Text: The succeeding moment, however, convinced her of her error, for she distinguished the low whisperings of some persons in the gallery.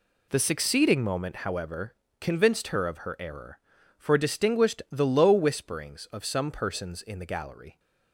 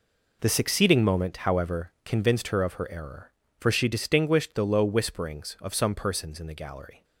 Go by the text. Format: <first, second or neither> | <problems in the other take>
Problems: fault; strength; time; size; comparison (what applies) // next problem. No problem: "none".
second | skips "she"; at 4.1 s